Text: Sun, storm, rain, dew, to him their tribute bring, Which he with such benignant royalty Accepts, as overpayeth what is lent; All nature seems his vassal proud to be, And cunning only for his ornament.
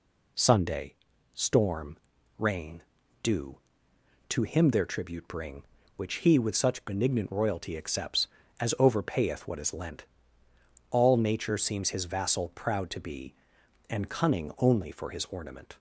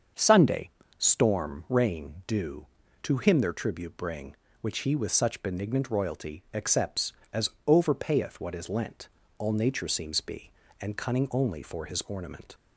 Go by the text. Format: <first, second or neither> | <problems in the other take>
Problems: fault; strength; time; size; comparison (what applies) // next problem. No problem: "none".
first | starts louder than the rest; until 1.4 s; 7 dB // pauses between "as" and "overpayeth"; slight; at 7.5 s; 0.16 s long // skips "his vassal proud to"; at 10.2 s